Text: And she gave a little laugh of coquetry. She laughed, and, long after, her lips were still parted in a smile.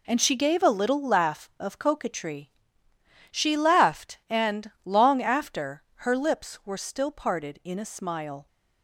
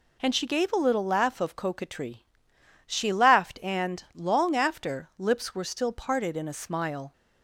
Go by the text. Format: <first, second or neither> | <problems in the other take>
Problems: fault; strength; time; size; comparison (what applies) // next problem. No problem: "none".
first | skips "her"; at 5.1 s